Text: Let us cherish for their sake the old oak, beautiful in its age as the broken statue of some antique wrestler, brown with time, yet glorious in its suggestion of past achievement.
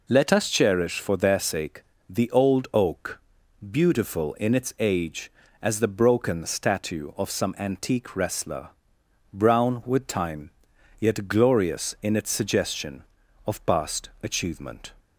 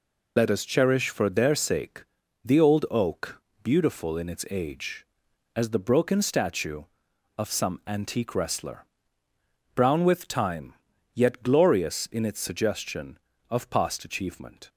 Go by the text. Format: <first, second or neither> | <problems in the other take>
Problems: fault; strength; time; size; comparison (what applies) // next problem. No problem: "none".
first | loses the start of "Let"; at 0.3 s; 90 ms // pauses between "sake" and "the"; at 2.0 s; 0.40 s long; slight in the first